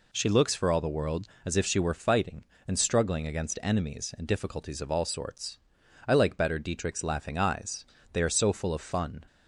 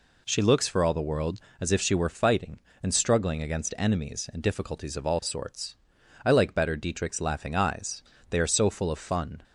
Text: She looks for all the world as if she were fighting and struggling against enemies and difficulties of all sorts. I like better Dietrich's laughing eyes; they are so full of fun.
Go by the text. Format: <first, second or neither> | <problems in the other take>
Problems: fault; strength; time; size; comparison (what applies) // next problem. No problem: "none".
neither | none